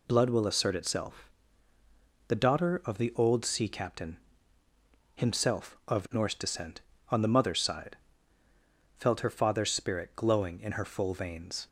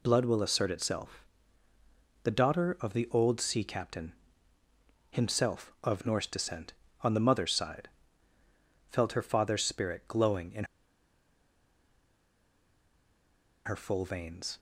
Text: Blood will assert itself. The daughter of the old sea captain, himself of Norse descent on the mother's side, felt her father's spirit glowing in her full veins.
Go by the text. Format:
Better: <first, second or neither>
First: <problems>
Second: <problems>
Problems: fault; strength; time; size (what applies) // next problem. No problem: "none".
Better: first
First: none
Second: pauses between "in" and "her"; strong; at 10.6 s; 3.0 s long